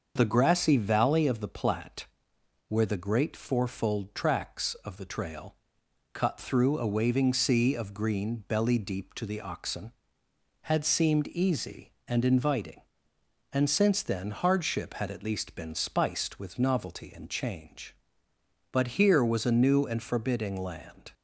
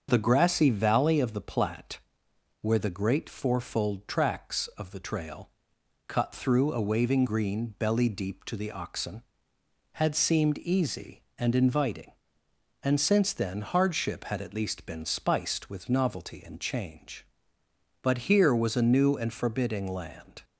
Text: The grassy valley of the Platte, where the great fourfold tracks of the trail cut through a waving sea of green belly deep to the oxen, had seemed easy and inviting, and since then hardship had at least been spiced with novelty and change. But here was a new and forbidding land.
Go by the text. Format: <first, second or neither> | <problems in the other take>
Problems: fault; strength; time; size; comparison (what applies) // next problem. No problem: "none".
first | starts louder than the rest; until 1.1 s; 7 dB; also in the first // pauses between "trail" and "cut"; noticeable; at 5.4 s; 0.58 s long; noticeable in the first // skips "sea of"; at 7.2 s